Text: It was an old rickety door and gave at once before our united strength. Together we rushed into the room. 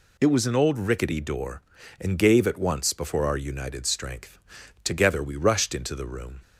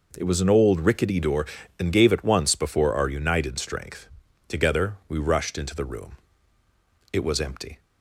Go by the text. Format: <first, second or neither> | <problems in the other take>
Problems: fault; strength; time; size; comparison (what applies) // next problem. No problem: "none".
first | goes on to say "It was empty"; noticeable; from 7.1 s on; 0.68 s long